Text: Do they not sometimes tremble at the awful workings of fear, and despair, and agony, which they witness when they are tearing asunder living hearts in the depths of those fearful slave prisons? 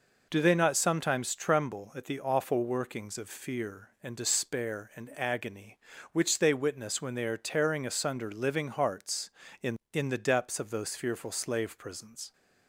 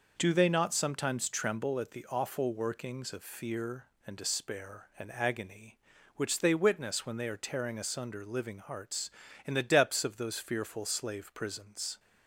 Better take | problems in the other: second | says "in" twice; at 9.9 s

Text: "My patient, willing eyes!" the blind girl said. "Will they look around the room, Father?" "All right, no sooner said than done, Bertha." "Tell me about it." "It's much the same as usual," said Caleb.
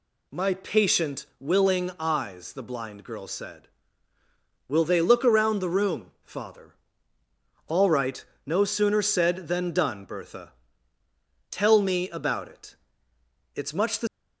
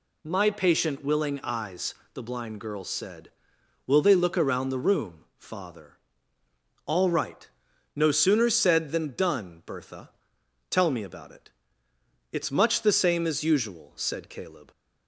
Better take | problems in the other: second | stops before "same as usual said Caleb"; at 14.0 s

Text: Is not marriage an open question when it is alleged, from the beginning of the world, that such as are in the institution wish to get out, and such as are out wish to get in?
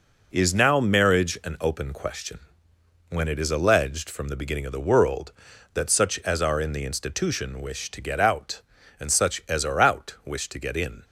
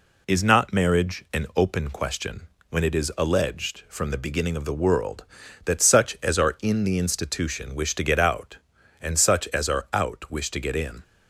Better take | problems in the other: second | says "now" for "not"; at 0.5 s // pauses between "question" and "when"; noticeable; at 2.4 s; 0.70 s long; slight in the second

